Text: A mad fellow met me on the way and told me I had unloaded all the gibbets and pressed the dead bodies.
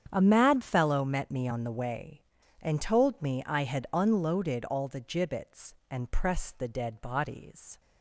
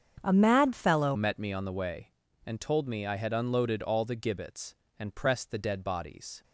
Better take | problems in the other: first | starts louder than the rest; strong; until 1.2 s; 7.5 dB; strong in the first // changes voice at "met"; from 1.1 s on; 5.3 s long

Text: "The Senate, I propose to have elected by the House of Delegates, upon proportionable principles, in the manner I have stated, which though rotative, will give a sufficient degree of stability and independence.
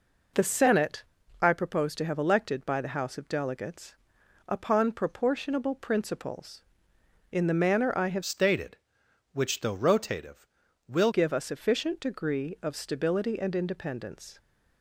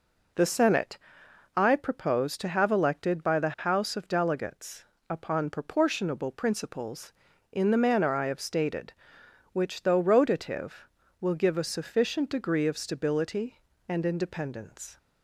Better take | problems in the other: second | changes voice from "stated" to "will"; from 8.2 to 11.1 s; 2.9 s long

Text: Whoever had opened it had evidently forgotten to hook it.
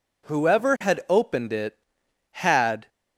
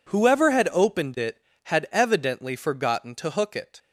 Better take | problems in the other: second | stops before "evidently forgotten to hook it"; at 2.8 s

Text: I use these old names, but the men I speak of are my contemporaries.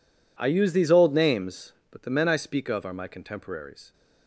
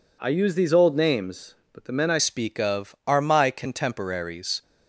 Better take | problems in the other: first | changes voice at "speak"; from 2.1 s on; 2.5 s long

